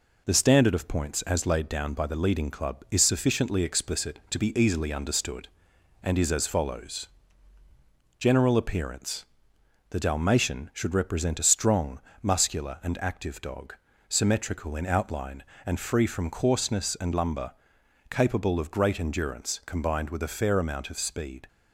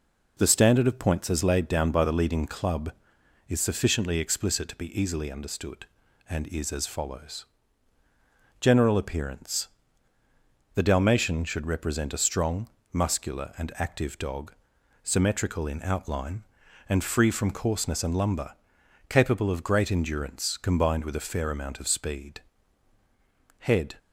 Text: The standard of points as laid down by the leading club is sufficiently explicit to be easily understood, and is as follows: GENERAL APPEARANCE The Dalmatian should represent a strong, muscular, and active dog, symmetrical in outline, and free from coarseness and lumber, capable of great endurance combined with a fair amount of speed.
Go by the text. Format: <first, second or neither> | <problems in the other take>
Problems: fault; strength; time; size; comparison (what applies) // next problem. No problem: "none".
first | pauses between "APPEARANCE" and "The"; at 9.6 s; 1.0 s long; noticeable in the first // goes on to say "HEAD"; slight; from 23.5 s on; 0.36 s long